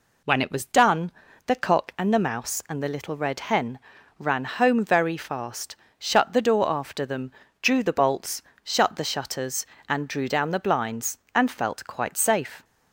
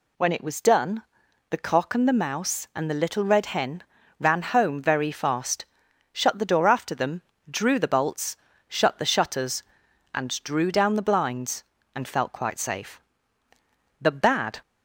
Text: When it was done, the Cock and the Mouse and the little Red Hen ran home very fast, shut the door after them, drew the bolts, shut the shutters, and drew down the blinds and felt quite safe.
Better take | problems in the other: first | pauses between "Hen" and "ran"; slight; at 3.8 s; 0.36 s long; also in the first // goes on to say "The bad"; noticeable; from 13.9 s on; 0.62 s long

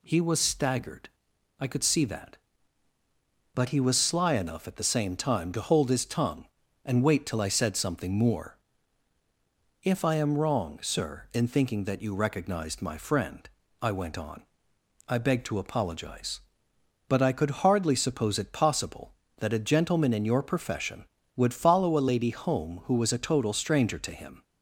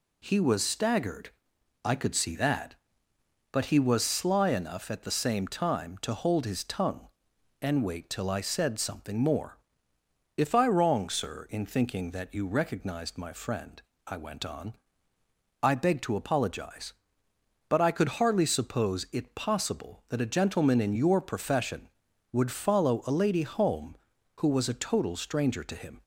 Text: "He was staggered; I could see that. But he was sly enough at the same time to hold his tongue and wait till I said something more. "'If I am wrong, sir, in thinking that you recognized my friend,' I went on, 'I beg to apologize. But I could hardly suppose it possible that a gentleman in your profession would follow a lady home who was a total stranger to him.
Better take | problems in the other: first | skips "am"; at 10.6 s

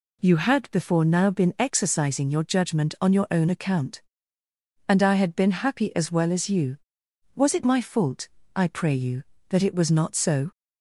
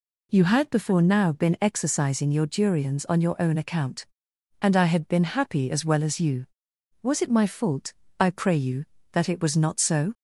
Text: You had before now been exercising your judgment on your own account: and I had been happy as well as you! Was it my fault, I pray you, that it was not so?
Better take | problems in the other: first | says "durians" for "judgment"; at 2.4 s

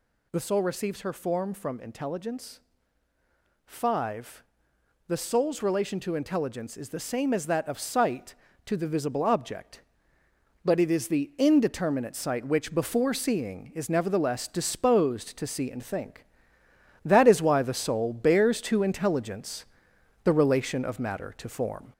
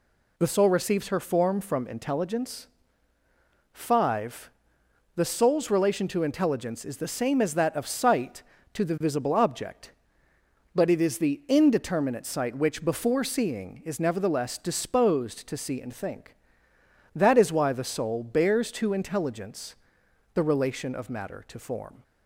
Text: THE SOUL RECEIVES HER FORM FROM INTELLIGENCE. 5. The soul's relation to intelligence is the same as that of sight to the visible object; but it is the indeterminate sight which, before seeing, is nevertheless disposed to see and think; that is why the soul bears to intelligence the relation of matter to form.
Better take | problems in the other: second | gets louder; throughout; 3.5 dB // pauses between "intelligence" and "the"; noticeable; at 19.6 s; 0.60 s long; noticeable in the second

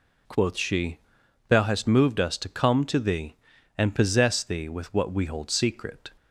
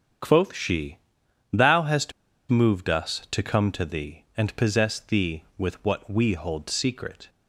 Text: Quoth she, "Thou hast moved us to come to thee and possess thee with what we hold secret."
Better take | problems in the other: first | starts louder than the rest; strong; until 1.7 s; 8 dB // pauses between "hast" and "moved"; at 2.1 s; 0.38 s long

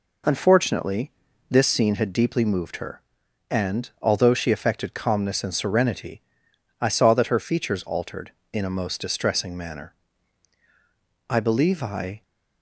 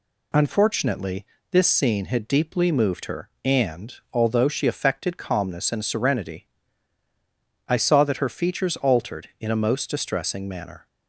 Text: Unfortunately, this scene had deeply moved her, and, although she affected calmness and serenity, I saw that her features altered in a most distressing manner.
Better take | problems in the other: second | goes on to say "I believe I"; noticeable; from 11.2 s on; 0.94 s long

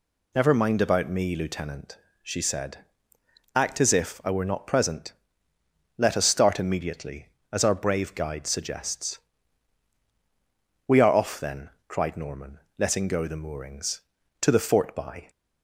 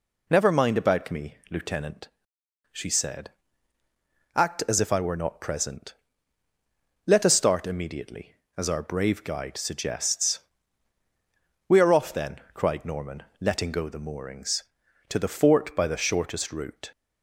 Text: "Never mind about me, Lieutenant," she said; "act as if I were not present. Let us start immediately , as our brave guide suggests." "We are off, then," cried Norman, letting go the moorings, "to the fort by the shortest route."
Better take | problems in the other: second | stops before "the shortest route"; at 15.2 s

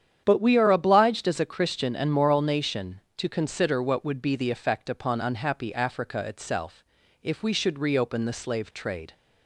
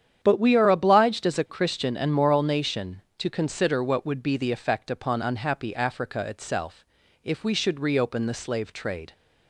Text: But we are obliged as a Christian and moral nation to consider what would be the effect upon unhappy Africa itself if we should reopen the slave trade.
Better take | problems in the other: neither | starts louder than the rest; strong; the same in both // pauses between "itself" and "if"; the same in both

